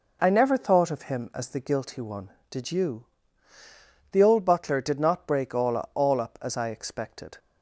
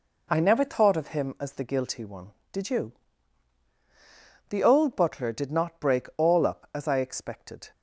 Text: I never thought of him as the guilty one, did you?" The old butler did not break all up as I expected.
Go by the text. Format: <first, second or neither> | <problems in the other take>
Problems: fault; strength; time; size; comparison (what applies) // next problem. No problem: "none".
second | says "all" twice; at 5.9 s